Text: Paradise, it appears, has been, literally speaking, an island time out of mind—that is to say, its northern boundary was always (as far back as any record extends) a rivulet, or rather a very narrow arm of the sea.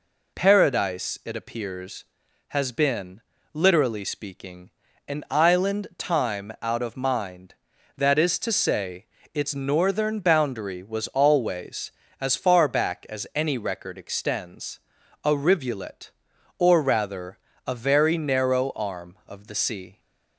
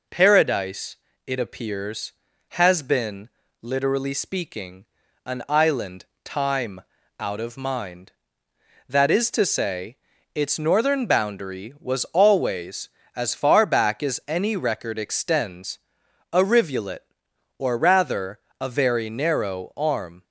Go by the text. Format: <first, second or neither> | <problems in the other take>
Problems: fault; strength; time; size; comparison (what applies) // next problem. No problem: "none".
first | pauses between "island" and "time"; slight; at 6.0 s; 0.18 s long // pauses between "time" and "out"; at 6.8 s; 0.38 s long // pauses between "rather" and "a"; slight; at 18.3 s; 0.20 s long; slight in the first // stops before "of the sea"; at 20.2 s